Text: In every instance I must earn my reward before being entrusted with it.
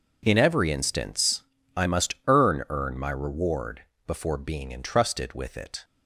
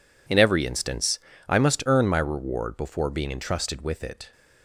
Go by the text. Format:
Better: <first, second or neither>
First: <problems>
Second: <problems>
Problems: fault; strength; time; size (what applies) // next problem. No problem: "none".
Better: second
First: pauses between "instance" and "I"; slight; at 1.4 s; 0.34 s long // says "earn" twice; at 2.6 s // pauses between "reward" and "before"; slight; at 3.8 s; 0.24 s long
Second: pauses between "instance" and "I"; slight; at 1.1 s; 0.28 s long